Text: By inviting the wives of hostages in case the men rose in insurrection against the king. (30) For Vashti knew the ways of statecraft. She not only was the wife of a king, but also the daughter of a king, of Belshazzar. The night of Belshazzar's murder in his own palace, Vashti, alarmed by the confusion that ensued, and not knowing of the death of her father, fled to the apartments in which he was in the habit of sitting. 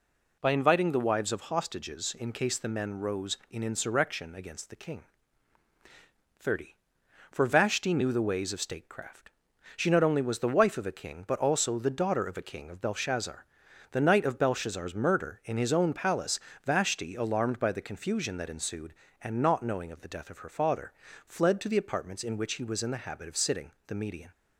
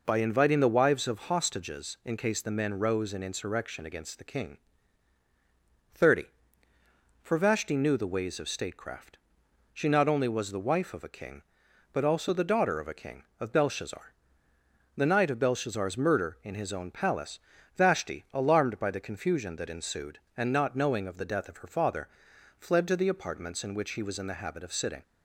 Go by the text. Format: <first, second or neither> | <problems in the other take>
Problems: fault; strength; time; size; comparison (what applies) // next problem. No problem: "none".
second | goes on to say "The Median"; slight; from 23.8 s on; 0.42 s long